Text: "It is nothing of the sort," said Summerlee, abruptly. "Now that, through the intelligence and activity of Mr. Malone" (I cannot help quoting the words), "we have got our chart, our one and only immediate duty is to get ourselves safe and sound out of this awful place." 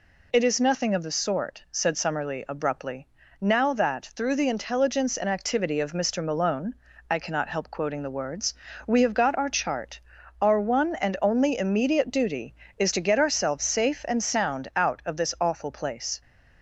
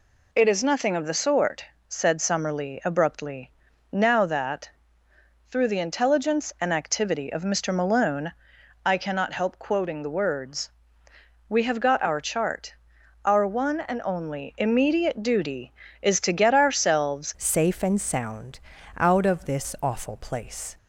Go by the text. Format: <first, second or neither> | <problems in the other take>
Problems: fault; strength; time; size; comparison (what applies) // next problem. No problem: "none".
first | changes voice at "safe"; from 17.3 s on; 3.4 s long // pauses between "sound" and "out"; at 18.5 s; 0.38 s long